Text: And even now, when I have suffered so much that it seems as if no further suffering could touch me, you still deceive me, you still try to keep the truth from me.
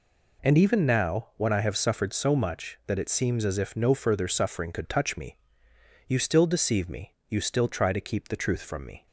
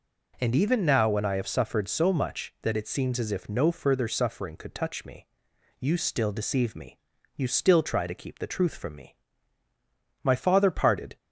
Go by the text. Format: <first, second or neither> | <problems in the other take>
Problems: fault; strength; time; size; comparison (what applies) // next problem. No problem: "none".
first | goes on to say "My father parted"; noticeable; from 10.2 s on; 0.94 s long